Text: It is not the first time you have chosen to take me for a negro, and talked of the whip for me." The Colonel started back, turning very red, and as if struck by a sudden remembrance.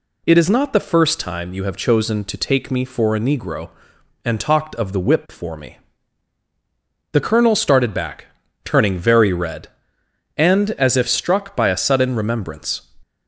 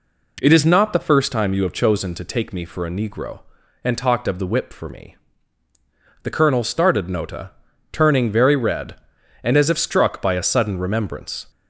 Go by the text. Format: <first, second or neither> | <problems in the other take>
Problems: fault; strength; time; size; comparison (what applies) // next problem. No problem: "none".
first | says "nota" for "back"; at 7.0 s